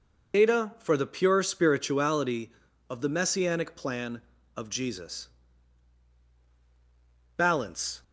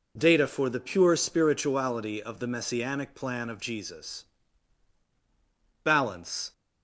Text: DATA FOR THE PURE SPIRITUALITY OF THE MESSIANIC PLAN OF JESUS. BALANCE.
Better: second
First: loses the start of "DATA"; at 0.3 s; 90 ms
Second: none

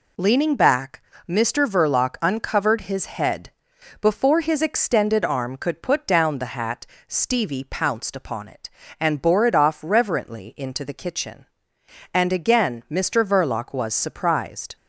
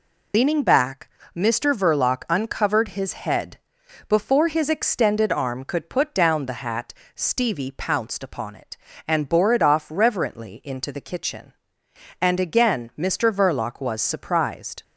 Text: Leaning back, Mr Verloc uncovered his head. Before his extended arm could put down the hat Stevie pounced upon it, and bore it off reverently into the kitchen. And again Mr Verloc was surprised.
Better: first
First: pauses between "hat" and "Stevie"; slight; at 6.8 s; 0.22 s long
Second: loses the start of "Leaning"; at 0.3 s; 100 ms // pauses between "hat" and "Stevie"; slight; at 6.9 s; 0.22 s long

